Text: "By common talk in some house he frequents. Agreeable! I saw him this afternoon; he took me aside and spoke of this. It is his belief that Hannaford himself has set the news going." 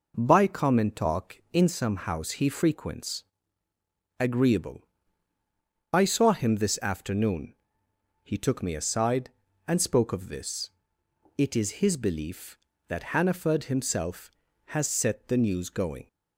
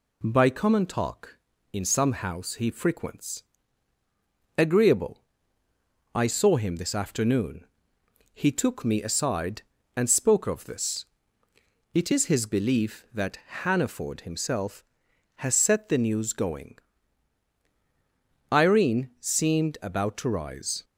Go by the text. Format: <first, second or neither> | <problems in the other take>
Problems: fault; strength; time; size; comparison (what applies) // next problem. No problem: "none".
first | pauses between "that" and "Hannaford"; slight; at 13.3 s; 0.24 s long // goes on to say "Irene seemed about to rise"; strong; from 18.5 s on; 2.3 s long